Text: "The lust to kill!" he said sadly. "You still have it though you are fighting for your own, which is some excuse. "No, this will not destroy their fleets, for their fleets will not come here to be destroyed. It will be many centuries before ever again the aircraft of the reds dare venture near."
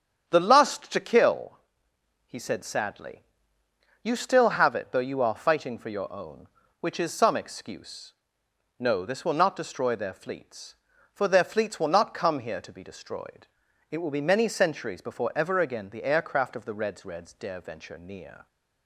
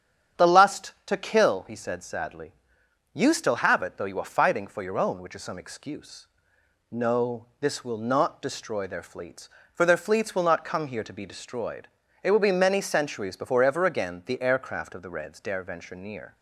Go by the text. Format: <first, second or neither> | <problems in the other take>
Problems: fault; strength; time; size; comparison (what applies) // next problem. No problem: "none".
second | starts louder than the rest; strong; until 1.3 s; 8.5 dB; strong in the second // says "reds" twice; at 17.0 s